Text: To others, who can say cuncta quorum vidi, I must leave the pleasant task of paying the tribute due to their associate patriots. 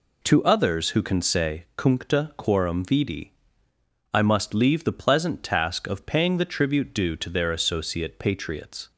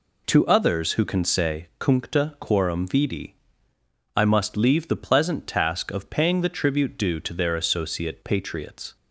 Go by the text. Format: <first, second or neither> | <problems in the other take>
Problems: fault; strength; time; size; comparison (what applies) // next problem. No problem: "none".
neither | none